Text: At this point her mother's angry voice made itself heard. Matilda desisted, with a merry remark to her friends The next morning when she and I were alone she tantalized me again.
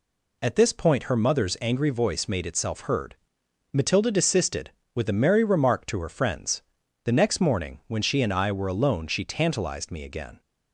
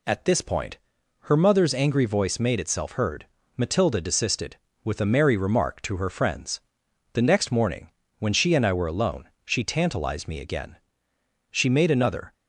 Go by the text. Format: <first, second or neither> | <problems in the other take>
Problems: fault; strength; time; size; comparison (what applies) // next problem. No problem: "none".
first | pauses between "point" and "her"; noticeable; at 0.7 s; 0.48 s long // pauses between "friends" and "The"; noticeable; at 6.5 s; 0.54 s long; also in the first // pauses between "morning" and "when"; slight; at 7.9 s; 0.28 s long // pauses between "alone" and "she"; slight; at 9.2 s; 0.16 s long // goes on to say "She made another"; noticeable; from 11.5 s on; 0.80 s long